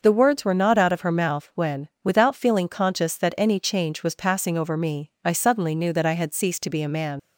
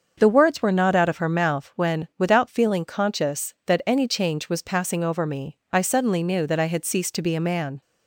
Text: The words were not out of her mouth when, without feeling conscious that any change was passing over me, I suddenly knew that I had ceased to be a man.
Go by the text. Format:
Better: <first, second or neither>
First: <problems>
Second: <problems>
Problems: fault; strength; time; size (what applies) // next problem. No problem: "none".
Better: second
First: starts louder than the rest; noticeable; until 1.0 s; 6 dB // leaves "man" unfinished; at 7.1 s; 75 ms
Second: starts louder than the rest; until 1.1 s; 6.5 dB